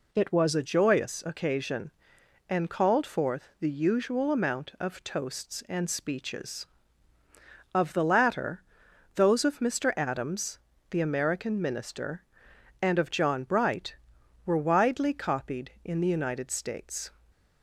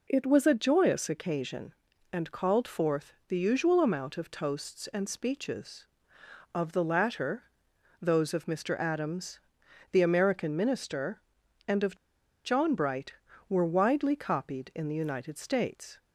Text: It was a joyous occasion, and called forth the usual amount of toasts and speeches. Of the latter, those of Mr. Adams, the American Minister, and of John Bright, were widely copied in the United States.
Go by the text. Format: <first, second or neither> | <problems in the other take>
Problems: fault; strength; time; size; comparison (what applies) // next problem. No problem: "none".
first | pauses between "forth" and "the"; slight; at 3.1 s; 0.16 s long // pauses between "of" and "John"; noticeable; at 11.9 s; 0.50 s long